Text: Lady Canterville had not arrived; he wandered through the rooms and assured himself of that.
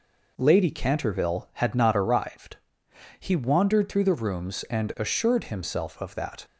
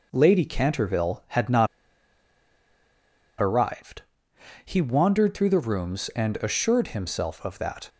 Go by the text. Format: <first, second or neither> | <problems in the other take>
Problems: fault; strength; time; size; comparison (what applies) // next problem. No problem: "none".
first | pauses between "not" and "arrived"; strong; at 1.6 s; 1.7 s long